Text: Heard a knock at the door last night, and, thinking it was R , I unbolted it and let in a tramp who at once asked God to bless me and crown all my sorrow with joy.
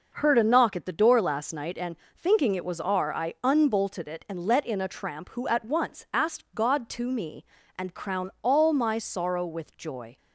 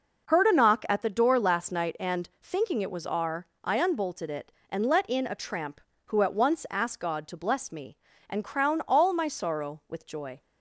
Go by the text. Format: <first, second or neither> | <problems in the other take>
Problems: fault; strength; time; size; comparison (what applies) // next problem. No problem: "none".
second | skips "bless"; at 7.1 s